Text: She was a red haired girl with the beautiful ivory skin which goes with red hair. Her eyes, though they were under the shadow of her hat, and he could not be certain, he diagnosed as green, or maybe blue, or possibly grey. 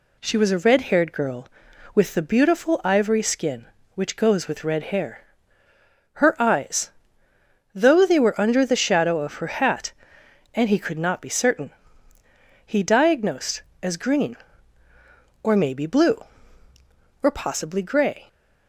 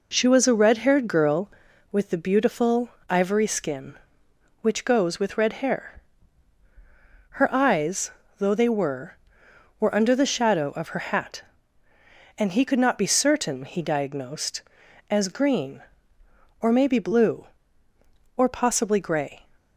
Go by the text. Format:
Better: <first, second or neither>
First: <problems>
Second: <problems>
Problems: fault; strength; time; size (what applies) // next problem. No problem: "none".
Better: first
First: none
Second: pauses between "beautiful" and "ivory"; slight; at 2.8 s; 0.18 s long // says "were" twice; at 9.7 s